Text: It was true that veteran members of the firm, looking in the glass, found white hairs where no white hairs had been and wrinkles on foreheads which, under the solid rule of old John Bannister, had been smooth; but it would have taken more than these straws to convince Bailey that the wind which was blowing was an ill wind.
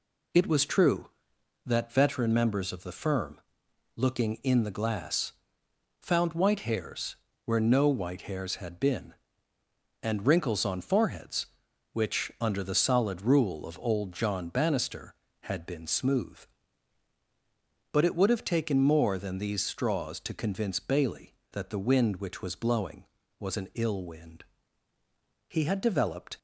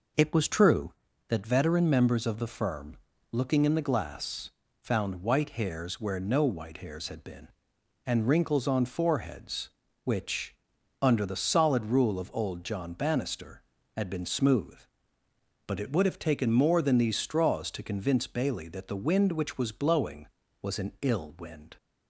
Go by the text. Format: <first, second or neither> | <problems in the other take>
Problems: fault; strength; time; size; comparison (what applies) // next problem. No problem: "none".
second | pauses between "hairs" and "where"; slight; at 7.1 s; 0.30 s long // goes on to say "He had developed"; noticeable; from 25.4 s on; 0.90 s long